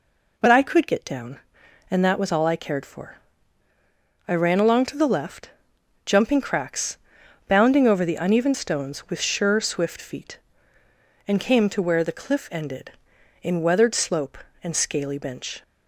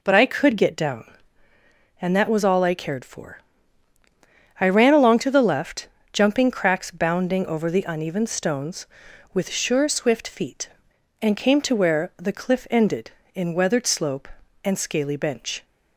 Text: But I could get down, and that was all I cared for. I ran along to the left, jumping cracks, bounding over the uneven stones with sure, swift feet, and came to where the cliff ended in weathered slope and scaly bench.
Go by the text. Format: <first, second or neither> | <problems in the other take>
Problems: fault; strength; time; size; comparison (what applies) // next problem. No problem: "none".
neither | none